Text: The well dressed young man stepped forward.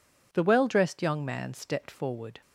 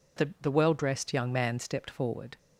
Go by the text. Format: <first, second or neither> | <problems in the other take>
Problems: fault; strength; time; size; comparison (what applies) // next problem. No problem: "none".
first | says "The" twice; at 0.4 s